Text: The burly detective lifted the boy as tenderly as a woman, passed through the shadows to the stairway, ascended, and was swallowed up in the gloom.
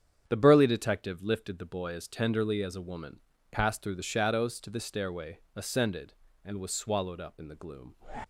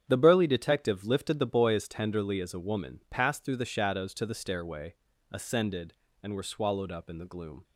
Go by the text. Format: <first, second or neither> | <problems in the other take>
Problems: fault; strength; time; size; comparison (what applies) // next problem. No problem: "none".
first | starts louder than the rest; strong; until 1.1 s; 8.5 dB; strong in the first // says "were" for "was"; at 6.3 s